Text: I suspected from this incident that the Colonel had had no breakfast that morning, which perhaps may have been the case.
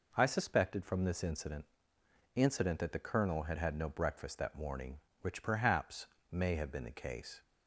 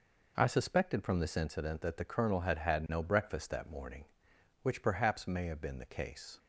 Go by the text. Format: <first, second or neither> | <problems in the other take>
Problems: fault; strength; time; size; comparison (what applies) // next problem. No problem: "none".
second | says "incident" twice; at 2.3 s // pauses between "perhaps" and "may"; slight; at 6.0 s; 0.24 s long